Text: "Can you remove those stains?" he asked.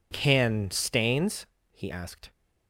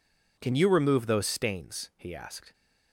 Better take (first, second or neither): second